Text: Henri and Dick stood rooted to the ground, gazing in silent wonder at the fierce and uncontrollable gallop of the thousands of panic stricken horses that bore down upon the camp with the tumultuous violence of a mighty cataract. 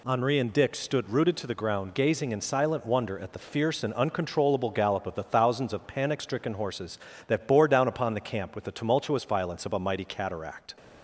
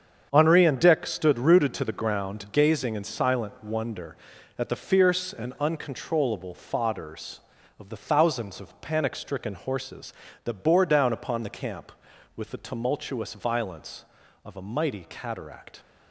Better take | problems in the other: first | starts louder than the rest; strong; until 1.3 s; 7.5 dB // says "fodders" for "gallop"; at 6.5 s

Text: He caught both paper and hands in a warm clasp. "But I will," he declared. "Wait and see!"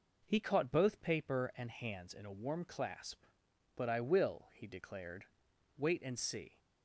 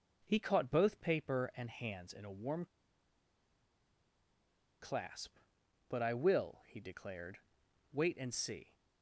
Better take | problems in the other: first | pauses between "warm" and "clasp"; strong; at 2.6 s; 2.1 s long

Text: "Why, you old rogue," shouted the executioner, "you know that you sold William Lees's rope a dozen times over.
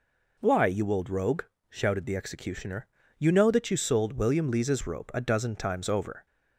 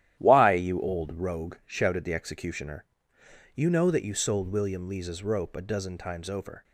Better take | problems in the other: first | gets quieter; strong; throughout; 9.5 dB

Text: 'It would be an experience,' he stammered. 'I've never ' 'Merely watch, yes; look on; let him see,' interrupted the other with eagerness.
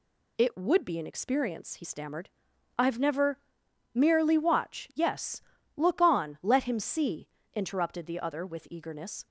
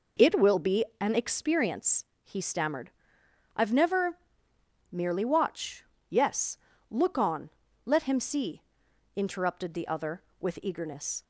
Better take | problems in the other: first | says "will" for "would"; at 0.3 s // pauses between "be" and "an"; slight; at 0.8 s; 0.15 s long

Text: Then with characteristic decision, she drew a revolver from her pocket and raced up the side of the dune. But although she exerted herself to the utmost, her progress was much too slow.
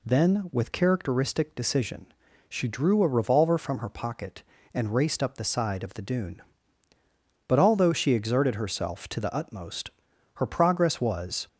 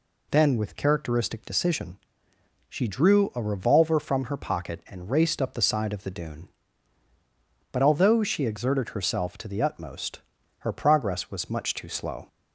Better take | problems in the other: second | stops before "much too slow"; at 11.4 s

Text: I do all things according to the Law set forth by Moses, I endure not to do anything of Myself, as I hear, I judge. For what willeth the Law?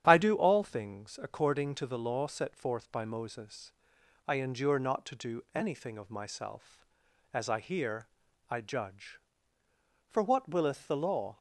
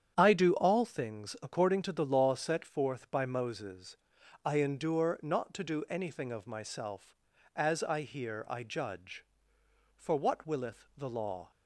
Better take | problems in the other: neither | starts louder than the rest; strong; the same in both

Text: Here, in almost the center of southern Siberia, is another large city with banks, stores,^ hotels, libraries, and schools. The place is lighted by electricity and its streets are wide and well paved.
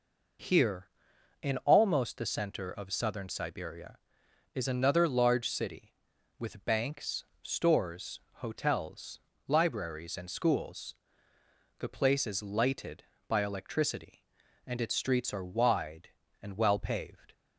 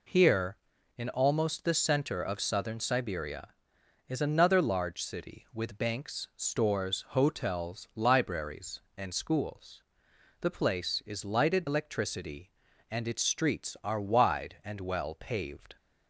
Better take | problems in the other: first | skips "by"; at 11.6 s

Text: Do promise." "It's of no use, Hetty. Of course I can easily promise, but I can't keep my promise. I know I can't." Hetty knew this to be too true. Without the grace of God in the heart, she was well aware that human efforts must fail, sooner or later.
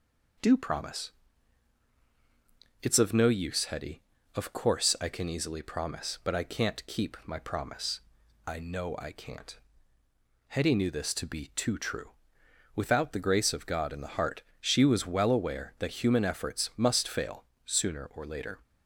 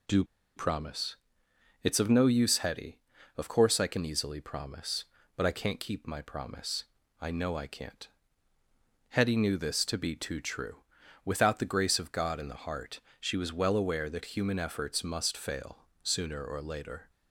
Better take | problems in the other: first | pauses between "Do" and "promise"; slight; at 0.2 s; 0.32 s long

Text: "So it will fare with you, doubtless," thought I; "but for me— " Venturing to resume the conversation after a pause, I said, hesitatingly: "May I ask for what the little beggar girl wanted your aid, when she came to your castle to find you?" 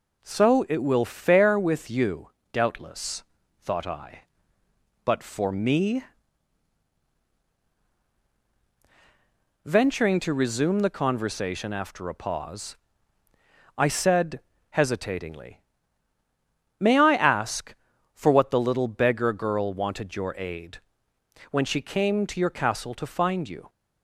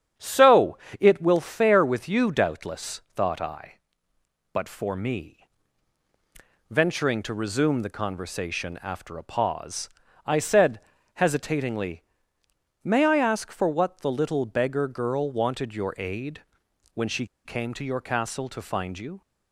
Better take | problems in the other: first | starts louder than the rest; strong; until 1.4 s; 11.5 dB // pauses between "So" and "it"; slight; at 0.7 s; 0.22 s long // pauses between "she" and "came"; slight; at 17.2 s; 0.18 s long

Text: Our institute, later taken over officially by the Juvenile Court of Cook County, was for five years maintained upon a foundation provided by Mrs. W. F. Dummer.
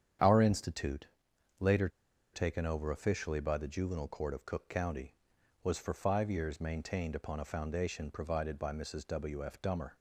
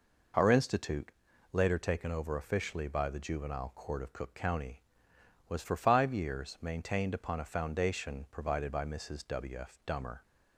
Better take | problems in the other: second | starts louder than the rest; strong; until 1.7 s; 8.5 dB // pauses between "later" and "taken"; at 1.8 s; 0.44 s long

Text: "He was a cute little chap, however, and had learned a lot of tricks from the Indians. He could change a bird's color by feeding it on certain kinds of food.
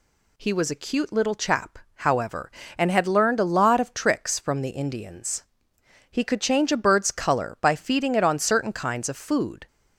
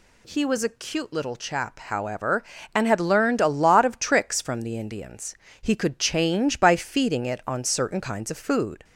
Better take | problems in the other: first | skips "a bird's color"; at 6.5 s

